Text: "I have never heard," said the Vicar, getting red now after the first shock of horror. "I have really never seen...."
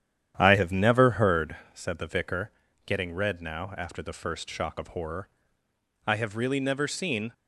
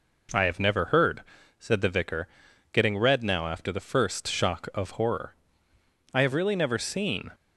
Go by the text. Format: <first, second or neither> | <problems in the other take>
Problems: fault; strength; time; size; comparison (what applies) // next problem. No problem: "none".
second | starts louder than the rest; strong; until 1.5 s; 9.5 dB